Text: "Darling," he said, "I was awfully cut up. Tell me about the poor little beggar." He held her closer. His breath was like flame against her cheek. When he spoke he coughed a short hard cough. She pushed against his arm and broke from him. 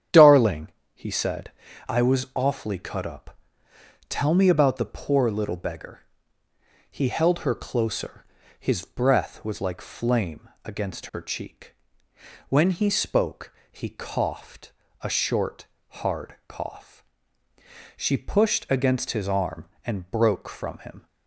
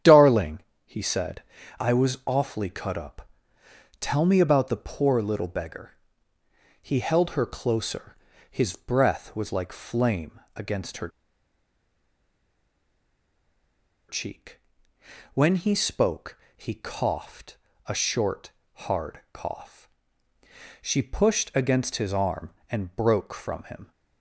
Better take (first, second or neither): first